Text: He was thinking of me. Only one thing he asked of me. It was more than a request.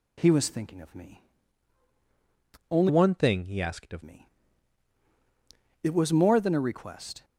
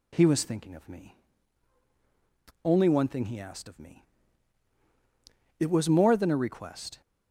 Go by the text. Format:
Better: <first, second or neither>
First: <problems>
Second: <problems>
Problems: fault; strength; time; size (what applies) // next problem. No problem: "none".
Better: second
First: changes voice from "one" to "of"; from 2.8 to 4.0 s; 1.2 s long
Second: none